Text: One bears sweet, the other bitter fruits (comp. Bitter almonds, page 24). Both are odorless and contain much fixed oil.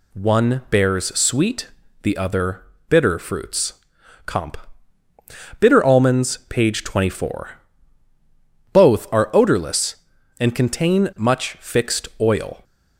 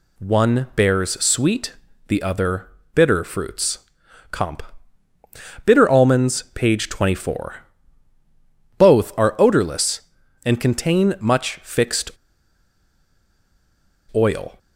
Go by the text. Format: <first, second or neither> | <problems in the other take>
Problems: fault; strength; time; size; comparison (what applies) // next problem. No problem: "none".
first | pauses between "other" and "bitter"; slight; at 2.6 s; 0.26 s long; slight in the first // pauses between "fixed" and "oil"; strong; at 12.1 s; 2.0 s long